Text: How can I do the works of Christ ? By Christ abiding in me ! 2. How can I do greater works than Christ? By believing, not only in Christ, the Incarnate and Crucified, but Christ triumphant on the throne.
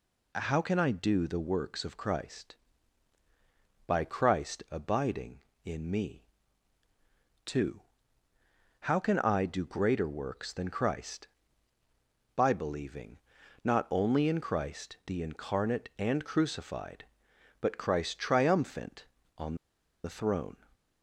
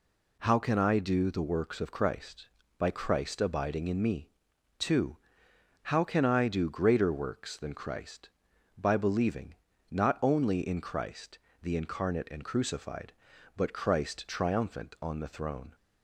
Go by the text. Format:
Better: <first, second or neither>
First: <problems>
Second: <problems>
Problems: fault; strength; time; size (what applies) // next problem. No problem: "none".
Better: second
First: pauses between "on" and "the"; noticeable; at 19.5 s; 0.47 s long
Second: none